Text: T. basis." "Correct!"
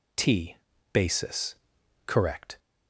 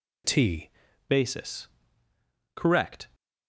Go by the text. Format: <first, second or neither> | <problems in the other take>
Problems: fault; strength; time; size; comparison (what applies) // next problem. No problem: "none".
first | changes voice at "basis"; from 1.0 s on; 2.0 s long